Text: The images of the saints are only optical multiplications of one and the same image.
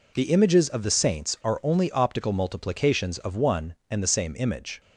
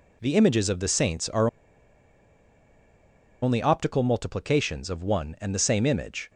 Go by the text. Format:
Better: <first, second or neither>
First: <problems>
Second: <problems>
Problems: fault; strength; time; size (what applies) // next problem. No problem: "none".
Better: first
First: none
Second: pauses between "are" and "only"; strong; at 1.4 s; 1.9 s long